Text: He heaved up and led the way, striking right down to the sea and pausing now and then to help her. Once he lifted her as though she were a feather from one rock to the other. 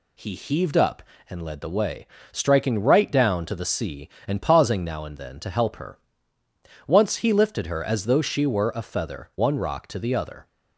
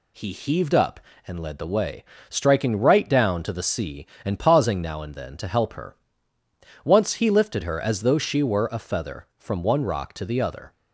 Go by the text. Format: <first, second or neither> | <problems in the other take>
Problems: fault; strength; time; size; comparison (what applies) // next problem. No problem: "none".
second | skips "from"; at 9.3 s